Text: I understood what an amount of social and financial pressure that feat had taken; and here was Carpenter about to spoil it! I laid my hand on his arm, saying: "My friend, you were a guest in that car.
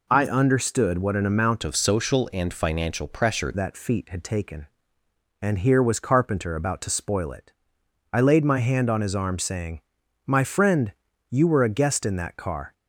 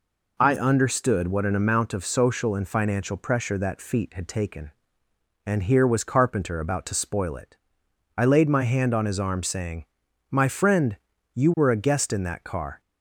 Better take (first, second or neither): second